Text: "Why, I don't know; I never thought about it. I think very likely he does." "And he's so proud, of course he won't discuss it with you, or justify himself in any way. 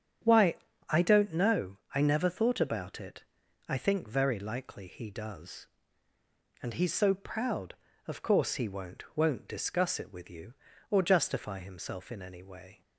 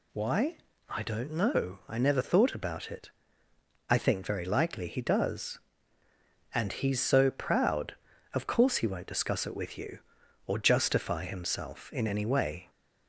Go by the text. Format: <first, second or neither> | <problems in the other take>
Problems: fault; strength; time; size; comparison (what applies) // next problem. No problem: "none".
second | starts louder than the rest; strong; until 1.5 s; 8.5 dB // says "won't" twice; at 9.1 s